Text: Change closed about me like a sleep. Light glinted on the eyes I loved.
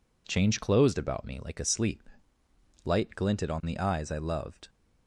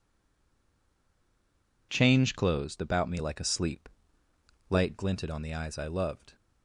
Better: first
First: none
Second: stays silent before the first word; noticeable; until 1.8 s; 1.8 s long

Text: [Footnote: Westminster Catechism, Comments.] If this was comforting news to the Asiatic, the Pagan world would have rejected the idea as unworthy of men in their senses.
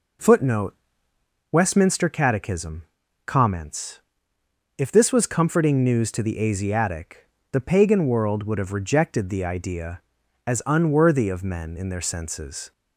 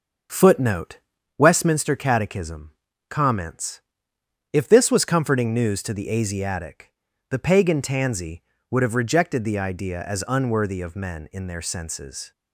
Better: first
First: none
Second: starts louder than the rest; until 1.7 s; 6.5 dB // says "tansy" for "world"; at 7.8 s

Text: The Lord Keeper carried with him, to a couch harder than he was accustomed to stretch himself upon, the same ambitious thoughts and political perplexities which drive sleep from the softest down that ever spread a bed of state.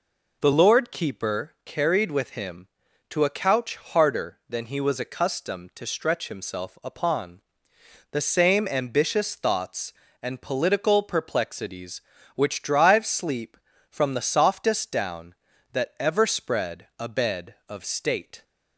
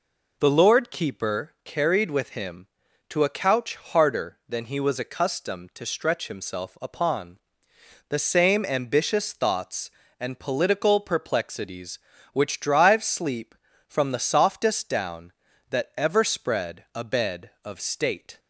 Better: neither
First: none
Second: none

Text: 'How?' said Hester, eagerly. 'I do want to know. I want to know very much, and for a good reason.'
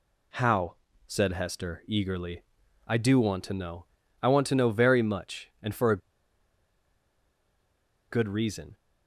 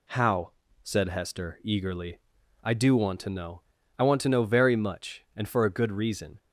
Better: second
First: pauses between "a" and "good"; strong; at 5.9 s; 2.1 s long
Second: none

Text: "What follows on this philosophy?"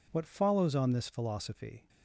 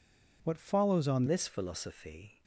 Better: first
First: none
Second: changes voice at "this"; from 1.2 s on; 1.2 s long

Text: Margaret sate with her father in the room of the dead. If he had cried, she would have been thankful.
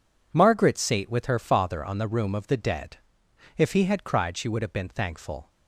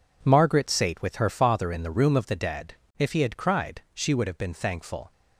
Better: second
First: says "on" for "in"; at 1.8 s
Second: none

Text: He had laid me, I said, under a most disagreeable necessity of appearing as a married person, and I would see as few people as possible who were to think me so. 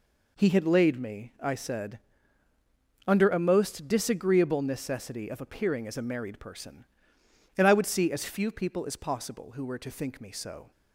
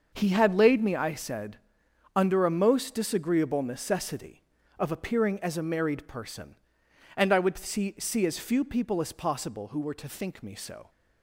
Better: first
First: none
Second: starts louder than the rest; until 1.1 s; 6.5 dB // says "see" twice; at 7.9 s

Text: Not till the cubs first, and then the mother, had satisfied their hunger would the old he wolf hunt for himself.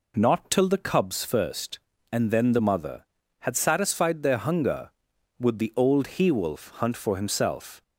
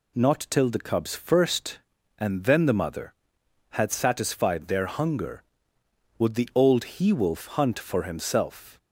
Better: neither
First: none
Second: none

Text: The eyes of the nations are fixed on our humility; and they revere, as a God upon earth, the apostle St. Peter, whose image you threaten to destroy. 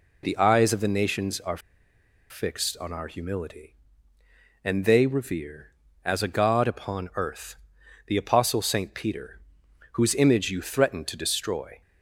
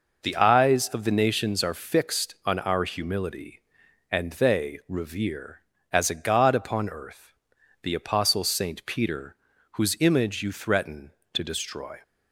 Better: second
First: pauses between "are" and "fixed"; noticeable; at 1.5 s; 0.71 s long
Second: none

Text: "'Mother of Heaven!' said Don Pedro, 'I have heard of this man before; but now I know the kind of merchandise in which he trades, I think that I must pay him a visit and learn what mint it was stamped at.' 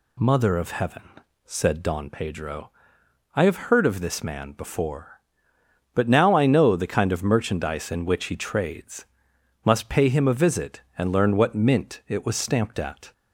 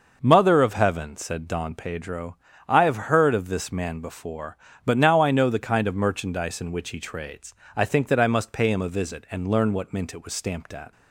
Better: second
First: skips "I think that I"; at 9.3 s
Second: none

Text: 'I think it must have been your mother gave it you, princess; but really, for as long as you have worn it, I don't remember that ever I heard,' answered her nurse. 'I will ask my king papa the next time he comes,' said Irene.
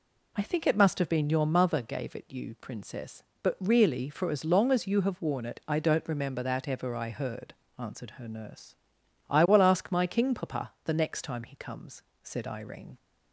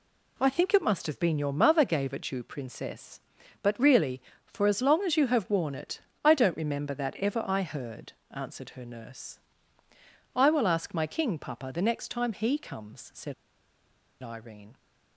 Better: first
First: none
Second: pauses between "said" and "Irene"; noticeable; at 13.3 s; 0.87 s long

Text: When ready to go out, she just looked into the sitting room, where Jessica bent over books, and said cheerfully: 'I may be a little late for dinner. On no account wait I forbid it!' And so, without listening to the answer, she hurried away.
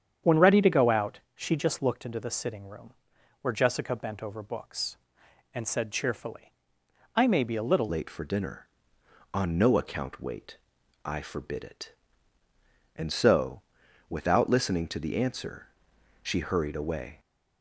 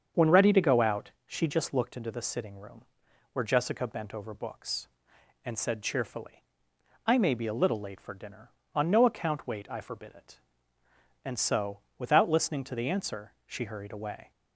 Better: second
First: starts louder than the rest; strong; until 1.4 s; 8 dB // changes voice at "late"; from 7.8 s on; 9.3 s long // pauses between "wait" and "I"; noticeable; at 10.5 s; 0.48 s long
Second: starts louder than the rest; strong; until 1.3 s; 7 dB

